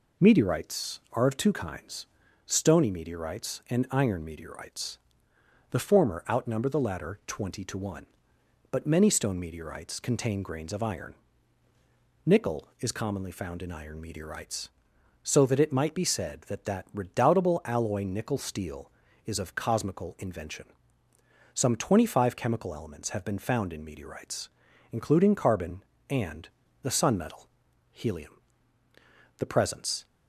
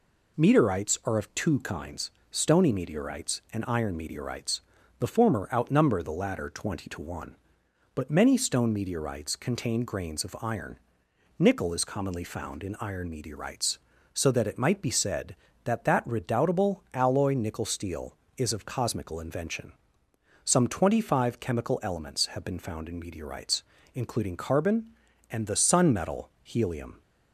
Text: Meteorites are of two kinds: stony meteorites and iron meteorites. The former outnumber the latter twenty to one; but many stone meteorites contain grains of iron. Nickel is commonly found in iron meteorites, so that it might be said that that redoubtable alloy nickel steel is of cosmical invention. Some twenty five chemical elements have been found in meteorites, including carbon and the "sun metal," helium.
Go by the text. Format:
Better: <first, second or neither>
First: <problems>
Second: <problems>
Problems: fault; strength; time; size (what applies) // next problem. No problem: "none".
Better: second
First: pauses between "and" and "the"; slight; at 26.4 s; 0.32 s long // goes on to say "The presence"; noticeable; from 29.3 s on; 0.68 s long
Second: none